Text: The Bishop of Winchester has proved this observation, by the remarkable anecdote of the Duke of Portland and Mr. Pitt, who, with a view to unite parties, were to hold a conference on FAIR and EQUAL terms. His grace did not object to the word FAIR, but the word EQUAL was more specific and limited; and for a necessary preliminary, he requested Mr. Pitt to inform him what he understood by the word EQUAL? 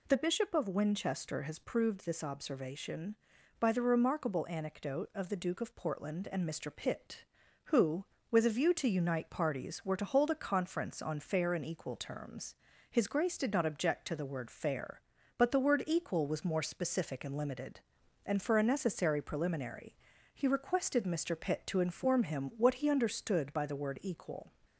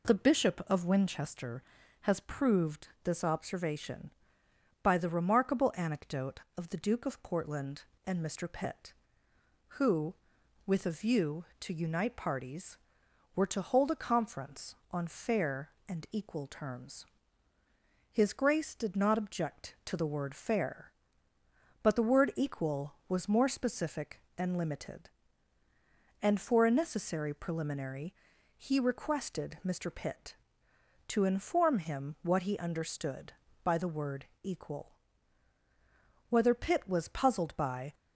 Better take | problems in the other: first | pauses between "word" and "EQUAL"; slight; at 34.2 s; 0.16 s long // goes on to say "Whether Pitt was puzzled by"; from 36.2 s on; 1.6 s long

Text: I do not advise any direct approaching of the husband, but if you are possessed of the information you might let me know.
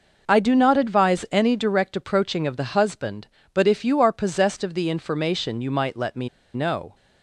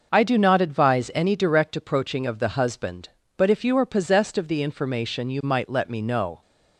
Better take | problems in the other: second | pauses between "me" and "know"; slight; at 6.2 s; 0.26 s long

